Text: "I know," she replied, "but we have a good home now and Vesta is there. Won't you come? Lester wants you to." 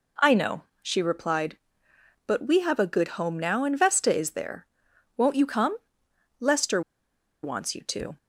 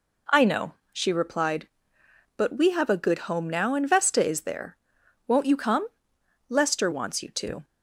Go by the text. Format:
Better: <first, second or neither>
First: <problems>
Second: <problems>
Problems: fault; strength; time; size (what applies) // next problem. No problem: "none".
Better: second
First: pauses between "Lester" and "wants"; noticeable; at 6.8 s; 0.62 s long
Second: none